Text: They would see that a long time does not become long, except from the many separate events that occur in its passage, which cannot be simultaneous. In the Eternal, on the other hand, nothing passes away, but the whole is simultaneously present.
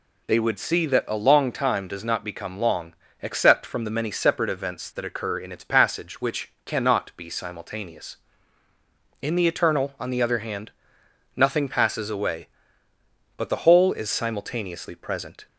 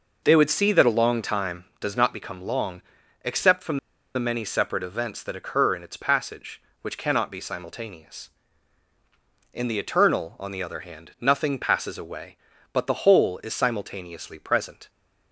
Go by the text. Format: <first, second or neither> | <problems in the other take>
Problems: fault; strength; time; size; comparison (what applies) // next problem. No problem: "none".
first | pauses between "from" and "the"; at 3.7 s; 0.37 s long